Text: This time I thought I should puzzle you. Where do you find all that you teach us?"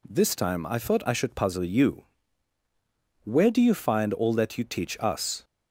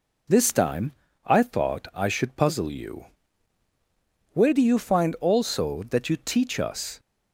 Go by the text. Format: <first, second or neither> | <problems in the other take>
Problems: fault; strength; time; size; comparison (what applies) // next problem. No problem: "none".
first | pauses between "time" and "I"; slight; at 0.9 s; 0.34 s long // says "also" for "all"; at 5.2 s